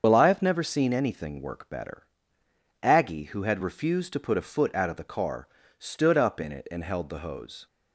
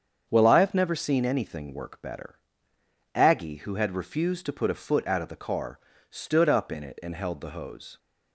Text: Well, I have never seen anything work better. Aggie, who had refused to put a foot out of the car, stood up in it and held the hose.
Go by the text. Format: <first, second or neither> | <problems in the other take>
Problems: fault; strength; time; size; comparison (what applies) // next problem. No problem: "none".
second | loses the start of "Well"; at 0.0 s; 65 ms // starts louder than the rest; until 1.0 s; 7 dB; strong in the second